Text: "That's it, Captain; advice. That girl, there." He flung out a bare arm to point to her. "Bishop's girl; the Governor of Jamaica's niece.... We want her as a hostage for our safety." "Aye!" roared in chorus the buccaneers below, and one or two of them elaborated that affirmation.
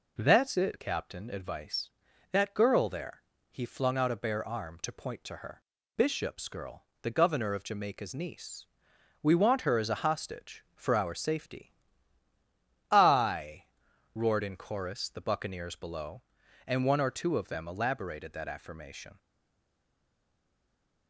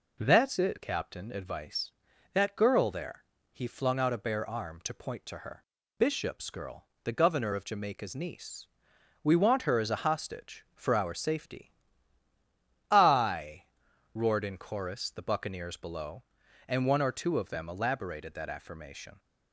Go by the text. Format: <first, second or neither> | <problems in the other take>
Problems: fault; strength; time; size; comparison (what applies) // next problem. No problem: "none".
second | stays silent after the last word; noticeable; from 19.1 s on; 1.9 s long